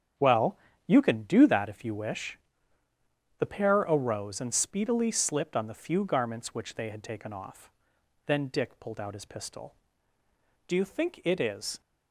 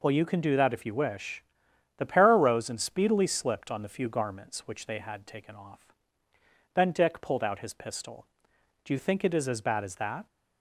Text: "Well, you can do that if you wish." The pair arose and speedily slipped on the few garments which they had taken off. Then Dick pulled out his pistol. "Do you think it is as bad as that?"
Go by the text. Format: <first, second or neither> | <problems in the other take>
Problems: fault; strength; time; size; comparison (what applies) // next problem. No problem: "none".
second | starts louder than the rest; strong; until 1.4 s; 8.5 dB // stops before "as bad as that"; at 11.8 s